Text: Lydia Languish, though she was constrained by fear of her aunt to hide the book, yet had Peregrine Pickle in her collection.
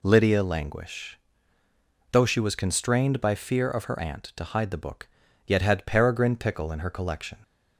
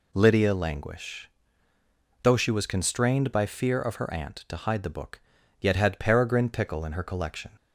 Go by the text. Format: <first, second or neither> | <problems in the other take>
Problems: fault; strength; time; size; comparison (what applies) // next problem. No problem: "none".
neither | none